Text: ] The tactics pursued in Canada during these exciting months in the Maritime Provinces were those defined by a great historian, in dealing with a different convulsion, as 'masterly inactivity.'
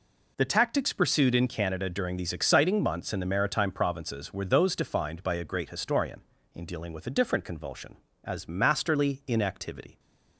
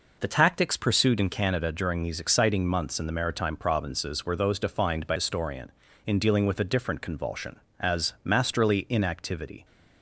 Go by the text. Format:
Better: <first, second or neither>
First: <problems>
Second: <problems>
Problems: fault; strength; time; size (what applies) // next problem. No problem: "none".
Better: first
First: none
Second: skips "a great"; at 5.1 s